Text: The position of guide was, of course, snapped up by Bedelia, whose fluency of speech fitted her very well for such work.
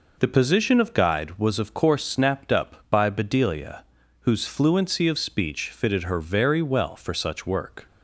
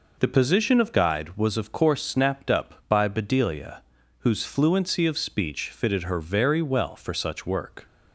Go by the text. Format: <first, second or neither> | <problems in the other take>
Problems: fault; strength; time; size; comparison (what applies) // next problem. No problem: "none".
neither | none